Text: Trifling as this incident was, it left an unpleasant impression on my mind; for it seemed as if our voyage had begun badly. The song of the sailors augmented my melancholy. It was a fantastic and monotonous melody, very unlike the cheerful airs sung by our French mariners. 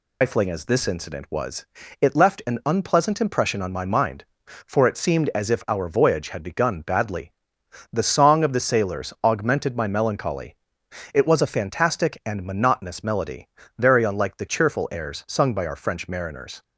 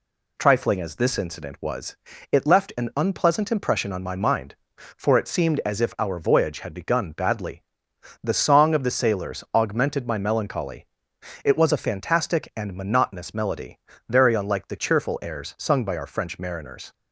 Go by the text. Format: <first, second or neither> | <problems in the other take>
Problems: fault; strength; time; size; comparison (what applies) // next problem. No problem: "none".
second | loses the start of "Trifling"; at 0.2 s; 125 ms